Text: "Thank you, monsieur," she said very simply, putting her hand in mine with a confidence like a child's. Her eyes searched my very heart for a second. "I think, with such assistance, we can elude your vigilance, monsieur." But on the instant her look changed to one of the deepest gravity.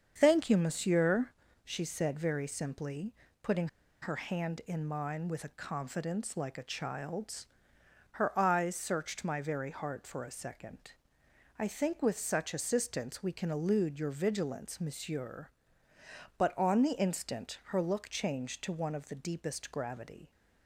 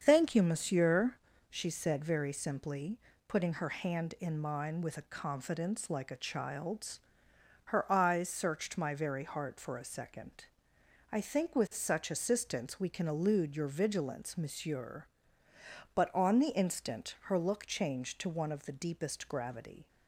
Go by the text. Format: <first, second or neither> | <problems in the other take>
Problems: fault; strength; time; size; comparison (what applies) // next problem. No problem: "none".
second | starts louder than the rest; strong; until 1.1 s; 7 dB; strong in the second // pauses between "putting" and "her"; slight; at 3.6 s; 0.35 s long